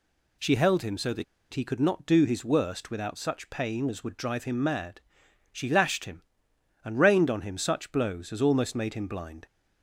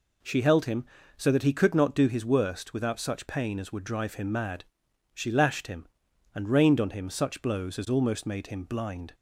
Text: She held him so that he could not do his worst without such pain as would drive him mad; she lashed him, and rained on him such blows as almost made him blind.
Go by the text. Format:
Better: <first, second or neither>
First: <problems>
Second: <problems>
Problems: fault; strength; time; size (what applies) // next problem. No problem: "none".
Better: second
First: pauses between "that" and "he"; slight; at 1.2 s; 0.28 s long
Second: none